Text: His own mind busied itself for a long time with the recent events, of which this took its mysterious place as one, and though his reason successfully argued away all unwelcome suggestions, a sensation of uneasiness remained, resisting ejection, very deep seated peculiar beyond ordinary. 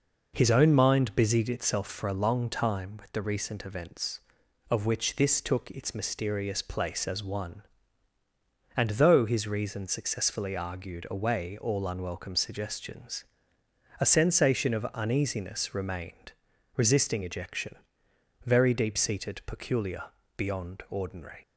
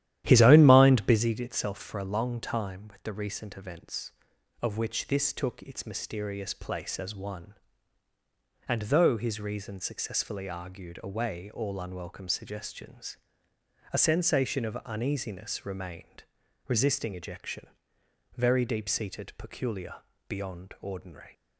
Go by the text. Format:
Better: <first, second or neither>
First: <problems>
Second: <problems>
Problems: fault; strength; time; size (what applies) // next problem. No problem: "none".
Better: first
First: pauses between "peculiar" and "beyond"; at 20.0 s; 0.38 s long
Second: starts louder than the rest; strong; until 1.2 s; 12 dB // pauses between "peculiar" and "beyond"; at 19.9 s; 0.38 s long